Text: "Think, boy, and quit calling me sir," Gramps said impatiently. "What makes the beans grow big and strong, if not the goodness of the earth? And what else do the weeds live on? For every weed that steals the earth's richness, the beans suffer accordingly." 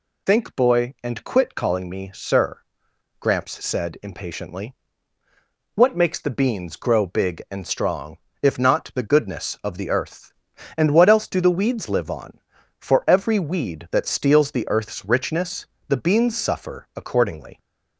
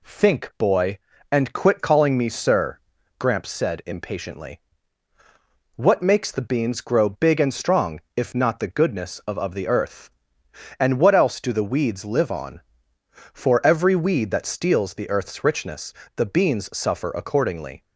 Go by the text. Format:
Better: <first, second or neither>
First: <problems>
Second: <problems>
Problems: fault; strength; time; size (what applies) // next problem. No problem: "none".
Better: first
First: none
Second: says "of" twice; at 9.3 s